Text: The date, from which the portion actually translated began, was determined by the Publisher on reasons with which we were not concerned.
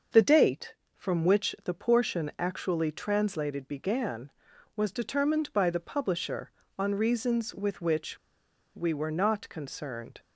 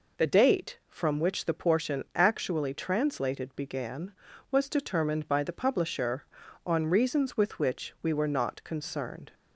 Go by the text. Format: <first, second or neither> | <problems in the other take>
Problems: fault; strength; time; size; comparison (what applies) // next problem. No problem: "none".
second | starts louder than the rest; until 1.3 s; 6.5 dB // pauses between "which" and "we"; noticeable; at 8.1 s; 0.58 s long